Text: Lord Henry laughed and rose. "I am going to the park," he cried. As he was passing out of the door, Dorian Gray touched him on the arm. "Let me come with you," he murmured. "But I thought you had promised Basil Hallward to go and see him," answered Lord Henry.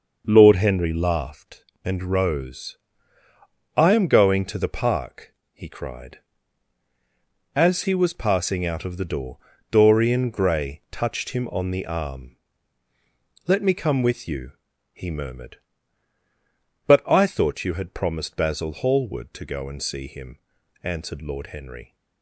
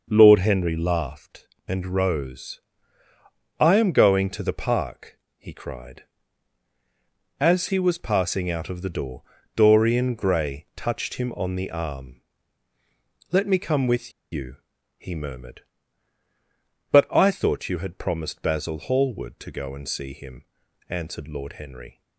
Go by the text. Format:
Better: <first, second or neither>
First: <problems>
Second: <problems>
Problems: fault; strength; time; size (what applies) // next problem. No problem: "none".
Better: first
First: none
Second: pauses between "with" and "you"; slight; at 14.1 s; 0.21 s long